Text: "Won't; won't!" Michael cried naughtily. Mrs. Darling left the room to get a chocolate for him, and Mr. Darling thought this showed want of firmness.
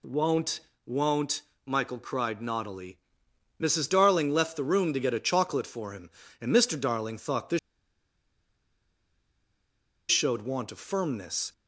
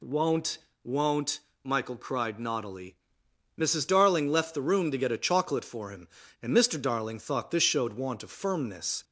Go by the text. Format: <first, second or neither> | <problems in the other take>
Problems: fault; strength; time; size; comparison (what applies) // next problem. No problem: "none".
second | pauses between "this" and "showed"; strong; at 7.5 s; 2.5 s long